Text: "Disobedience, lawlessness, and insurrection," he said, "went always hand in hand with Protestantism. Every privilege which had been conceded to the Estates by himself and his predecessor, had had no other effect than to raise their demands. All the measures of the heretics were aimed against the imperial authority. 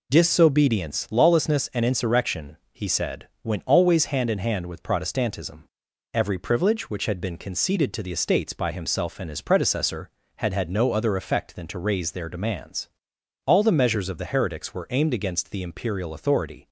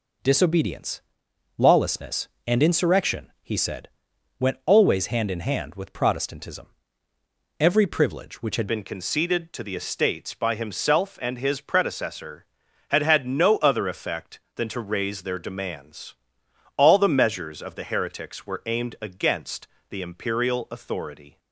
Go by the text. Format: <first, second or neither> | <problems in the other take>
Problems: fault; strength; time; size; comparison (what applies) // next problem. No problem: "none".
first | changes voice at "been"; from 8.6 s on; 12.7 s long // pauses between "against" and "the"; slight; at 19.6 s; 0.22 s long